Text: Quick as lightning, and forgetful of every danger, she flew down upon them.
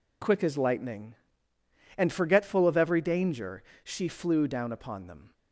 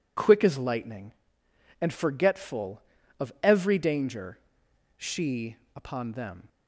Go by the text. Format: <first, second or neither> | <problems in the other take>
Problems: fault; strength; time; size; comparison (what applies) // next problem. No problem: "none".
first | skips "flew down"; at 5.6 s